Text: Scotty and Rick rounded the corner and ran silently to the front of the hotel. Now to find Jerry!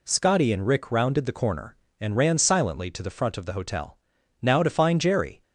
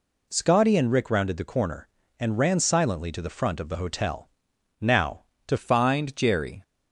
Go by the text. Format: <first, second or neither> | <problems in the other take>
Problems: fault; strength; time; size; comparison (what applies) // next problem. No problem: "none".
first | changes voice at "find"; from 5.5 s on; 1.1 s long